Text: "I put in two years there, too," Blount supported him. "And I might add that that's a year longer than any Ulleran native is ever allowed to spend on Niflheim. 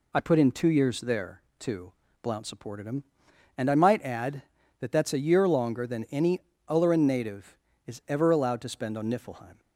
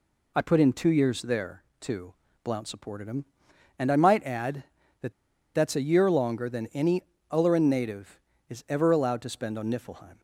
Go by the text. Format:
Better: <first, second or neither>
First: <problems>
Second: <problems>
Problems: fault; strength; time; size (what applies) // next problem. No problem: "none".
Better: first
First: pauses between "any" and "Ulleran"; slight; at 6.3 s; 0.28 s long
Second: pauses between "that" and "that's"; at 5.1 s; 0.41 s long // pauses between "any" and "Ulleran"; slight; at 7.0 s; 0.28 s long